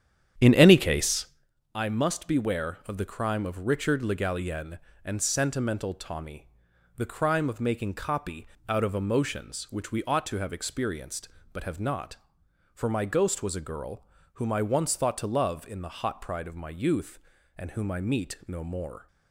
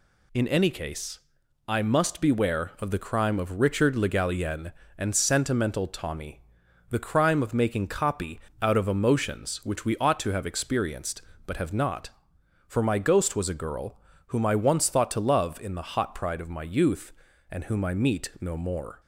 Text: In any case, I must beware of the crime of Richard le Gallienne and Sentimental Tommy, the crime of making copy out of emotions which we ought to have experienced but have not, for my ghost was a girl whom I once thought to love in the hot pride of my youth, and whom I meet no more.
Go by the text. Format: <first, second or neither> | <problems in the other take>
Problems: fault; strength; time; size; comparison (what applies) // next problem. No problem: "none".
second | starts louder than the rest; strong; until 1.5 s; 9.5 dB // pauses between "copy" and "out"; slight; at 8.4 s; 0.22 s long; slight in the second // pauses between "girl" and "whom"; slight; at 14.0 s; 0.30 s long; slight in the second